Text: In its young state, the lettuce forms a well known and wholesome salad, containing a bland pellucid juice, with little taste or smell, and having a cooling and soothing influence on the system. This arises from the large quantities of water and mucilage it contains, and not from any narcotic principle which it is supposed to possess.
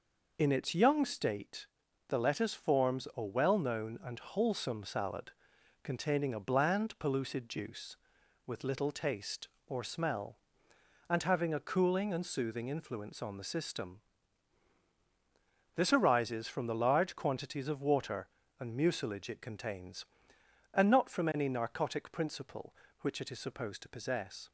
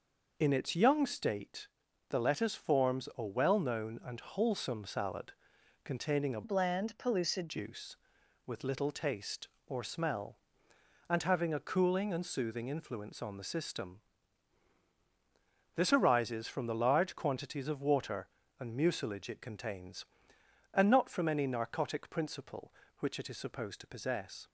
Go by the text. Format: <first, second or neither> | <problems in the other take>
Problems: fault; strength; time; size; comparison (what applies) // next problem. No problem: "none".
first | changes voice from "bland" to "pellucid"; from 6.4 to 7.4 s; 1.0 s long